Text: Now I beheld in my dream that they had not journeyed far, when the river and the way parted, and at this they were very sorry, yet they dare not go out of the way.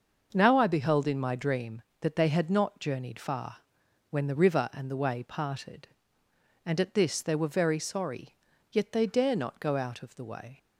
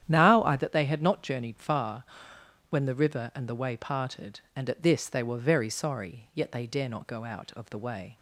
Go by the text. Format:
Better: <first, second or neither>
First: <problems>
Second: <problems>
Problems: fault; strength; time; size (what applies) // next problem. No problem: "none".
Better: first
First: starts louder than the rest; noticeable; until 1.3 s; 6 dB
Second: starts louder than the rest; strong; until 1.0 s; 10.5 dB // skips "beheld in my dream"; at 0.5 s